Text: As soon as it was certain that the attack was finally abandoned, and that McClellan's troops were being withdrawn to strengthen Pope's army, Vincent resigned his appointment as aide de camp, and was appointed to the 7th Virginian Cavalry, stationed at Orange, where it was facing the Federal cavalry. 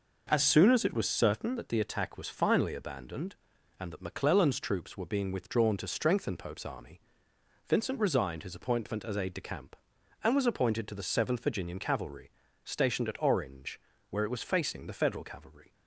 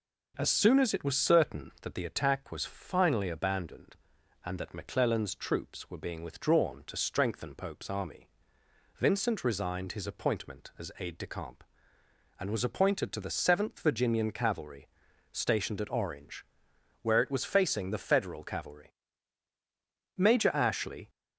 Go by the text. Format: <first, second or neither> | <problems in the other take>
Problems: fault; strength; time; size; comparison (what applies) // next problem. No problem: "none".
first | goes on to say "Major Ashley"; noticeable; from 20.1 s on; 0.92 s long